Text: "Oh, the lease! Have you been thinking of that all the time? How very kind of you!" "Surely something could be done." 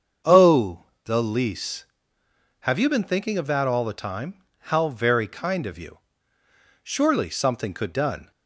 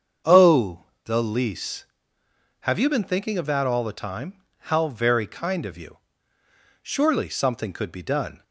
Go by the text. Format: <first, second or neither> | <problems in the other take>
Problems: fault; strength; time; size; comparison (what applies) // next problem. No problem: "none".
second | starts louder than the rest; until 1.4 s; 7 dB; also in the second // skips "be"; at 7.9 s